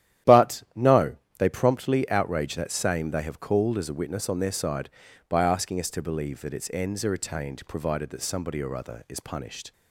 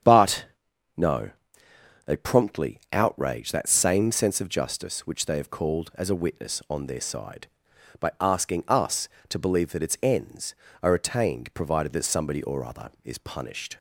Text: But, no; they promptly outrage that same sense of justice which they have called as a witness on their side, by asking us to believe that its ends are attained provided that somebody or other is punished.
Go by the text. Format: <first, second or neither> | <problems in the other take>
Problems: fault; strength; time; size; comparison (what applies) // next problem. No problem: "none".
second | starts louder than the rest; strong; until 1.6 s; 11.5 dB; strong in the second // skips "sense of justice which"; at 3.0 s